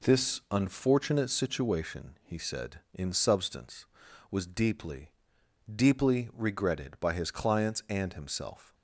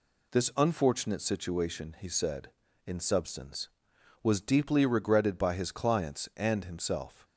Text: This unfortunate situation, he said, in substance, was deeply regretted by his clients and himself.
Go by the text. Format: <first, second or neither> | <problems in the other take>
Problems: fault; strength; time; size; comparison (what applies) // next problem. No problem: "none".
second | says "deeply" twice; at 5.7 s